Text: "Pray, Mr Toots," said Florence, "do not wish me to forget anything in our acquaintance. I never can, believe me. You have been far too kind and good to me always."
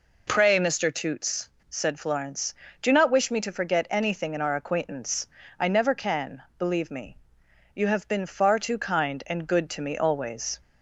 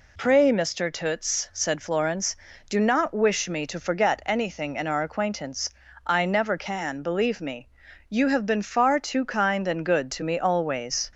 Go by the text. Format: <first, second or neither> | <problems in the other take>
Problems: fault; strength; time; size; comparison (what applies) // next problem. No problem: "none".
neither | none